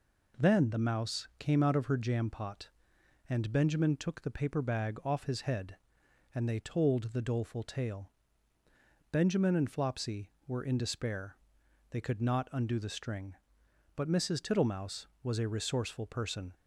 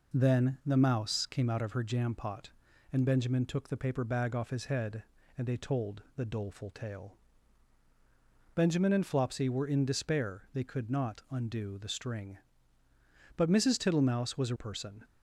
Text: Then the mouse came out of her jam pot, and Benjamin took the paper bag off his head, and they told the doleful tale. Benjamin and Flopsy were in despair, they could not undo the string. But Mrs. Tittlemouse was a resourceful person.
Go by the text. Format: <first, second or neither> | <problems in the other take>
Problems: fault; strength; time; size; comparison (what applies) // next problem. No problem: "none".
first | skips "resourceful"; at 14.5 s